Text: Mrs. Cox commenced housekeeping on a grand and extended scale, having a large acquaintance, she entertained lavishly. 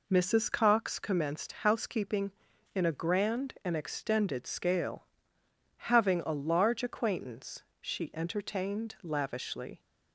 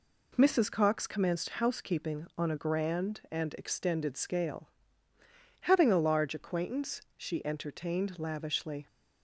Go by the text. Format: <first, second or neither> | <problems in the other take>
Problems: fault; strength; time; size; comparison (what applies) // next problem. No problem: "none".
second | says "in" for "on"; at 2.7 s